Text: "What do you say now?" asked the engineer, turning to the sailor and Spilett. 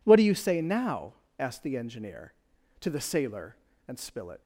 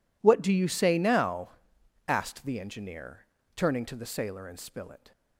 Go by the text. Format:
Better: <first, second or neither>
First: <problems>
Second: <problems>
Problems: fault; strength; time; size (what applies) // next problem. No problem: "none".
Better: second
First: skips "turning"; at 2.5 s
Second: none